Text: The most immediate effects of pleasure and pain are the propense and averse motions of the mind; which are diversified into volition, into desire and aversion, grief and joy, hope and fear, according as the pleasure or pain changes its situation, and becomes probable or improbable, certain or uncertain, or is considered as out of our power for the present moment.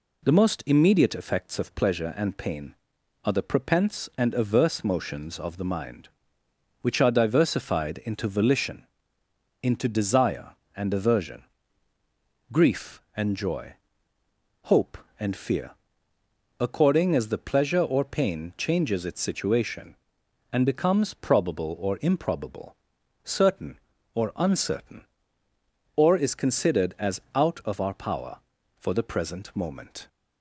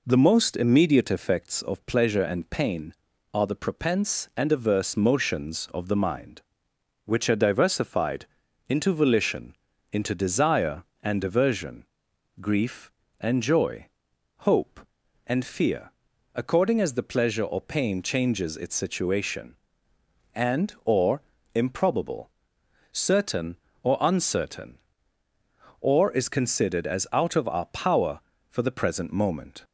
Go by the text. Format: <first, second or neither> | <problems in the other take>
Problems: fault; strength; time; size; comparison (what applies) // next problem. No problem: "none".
first | pauses between "diversified" and "into"; at 8.2 s; 0.42 s long // skips "becomes probable"; at 20.7 s // pauses between "or" and "improbable"; slight; at 21.2 s; 0.32 s long